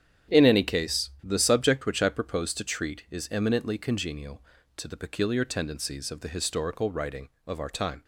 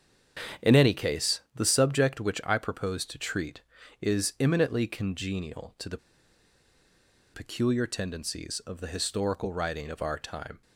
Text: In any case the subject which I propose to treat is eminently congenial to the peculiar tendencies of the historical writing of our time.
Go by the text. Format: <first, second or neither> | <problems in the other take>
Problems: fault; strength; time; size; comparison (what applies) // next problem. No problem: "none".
first | starts louder than the rest; strong; until 1.7 s; 8 dB; strong in the first // pauses between "case" and "the"; slight; at 1.3 s; 0.16 s long // pauses between "the" and "peculiar"; strong; at 5.9 s; 1.3 s long